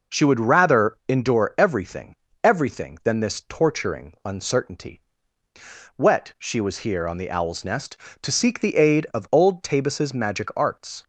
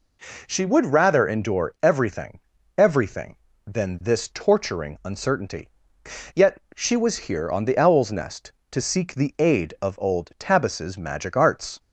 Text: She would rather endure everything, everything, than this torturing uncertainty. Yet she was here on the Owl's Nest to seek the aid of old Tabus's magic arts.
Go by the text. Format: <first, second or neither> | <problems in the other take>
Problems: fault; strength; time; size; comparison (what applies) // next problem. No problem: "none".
second | says "Wet" for "Yet"; at 5.9 s